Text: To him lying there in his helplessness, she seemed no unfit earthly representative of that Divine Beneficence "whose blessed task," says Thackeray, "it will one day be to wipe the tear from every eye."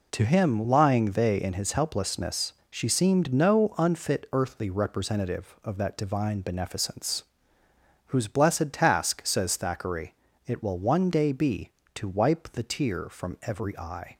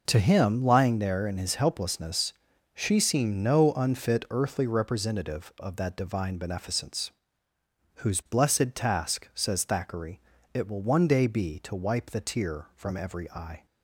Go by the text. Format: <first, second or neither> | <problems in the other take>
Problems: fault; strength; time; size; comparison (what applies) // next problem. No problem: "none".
second | says "they" for "there"; at 1.1 s // pauses between "Beneficence" and "whose"; noticeable; at 7.2 s; 0.86 s long; noticeable in the second